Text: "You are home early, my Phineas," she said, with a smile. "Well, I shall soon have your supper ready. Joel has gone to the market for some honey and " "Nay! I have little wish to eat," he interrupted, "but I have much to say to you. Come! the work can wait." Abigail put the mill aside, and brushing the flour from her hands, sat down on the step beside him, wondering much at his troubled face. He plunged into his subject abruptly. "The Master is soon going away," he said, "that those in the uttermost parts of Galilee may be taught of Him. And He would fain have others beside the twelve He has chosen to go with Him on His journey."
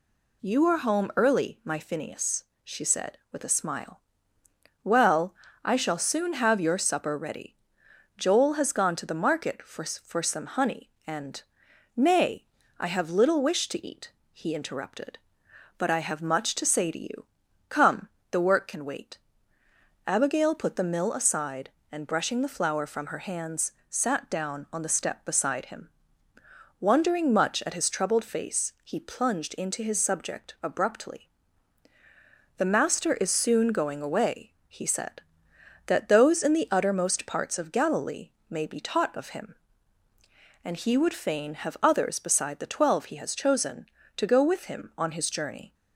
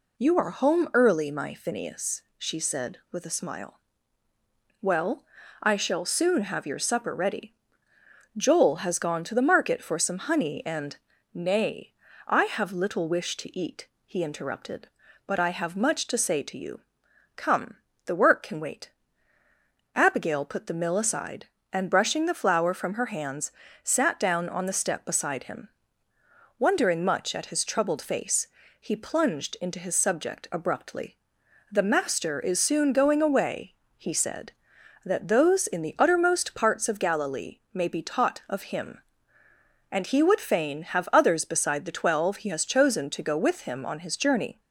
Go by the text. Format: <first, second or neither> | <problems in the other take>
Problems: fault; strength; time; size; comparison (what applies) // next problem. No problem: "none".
second | says "for" twice; at 9.8 s // pauses between "Galilee" and "may"; slight; at 38.2 s; 0.18 s long